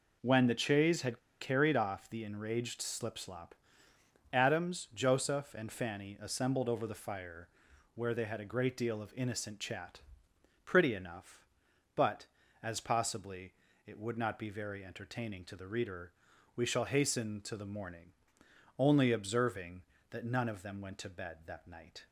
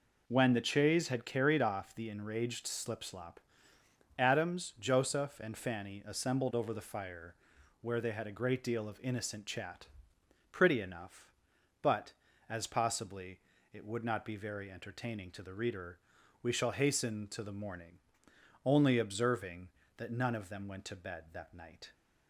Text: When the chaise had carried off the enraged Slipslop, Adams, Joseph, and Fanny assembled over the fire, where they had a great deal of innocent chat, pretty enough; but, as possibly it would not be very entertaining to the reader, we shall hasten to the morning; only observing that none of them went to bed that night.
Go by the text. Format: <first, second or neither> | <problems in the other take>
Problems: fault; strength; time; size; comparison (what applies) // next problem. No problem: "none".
second | pauses between "had" and "carried"; slight; at 1.1 s; 0.21 s long // pauses between "possibly" and "it"; slight; at 13.5 s; 0.32 s long; slight in the second